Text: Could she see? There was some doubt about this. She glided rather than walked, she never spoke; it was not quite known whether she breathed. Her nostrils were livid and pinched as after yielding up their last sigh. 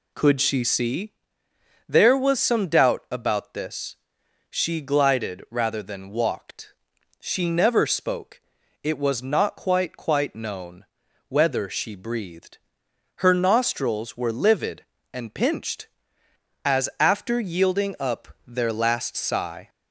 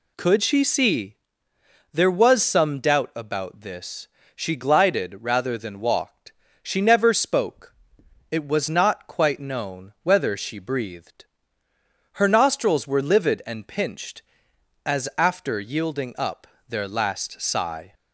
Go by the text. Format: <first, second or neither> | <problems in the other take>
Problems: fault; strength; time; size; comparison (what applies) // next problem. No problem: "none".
second | says "quite" twice; at 9.9 s // pauses between "known" and "whether"; at 10.8 s; 0.42 s long // pauses between "up" and "their"; slight; at 18.2 s; 0.18 s long; slight in the second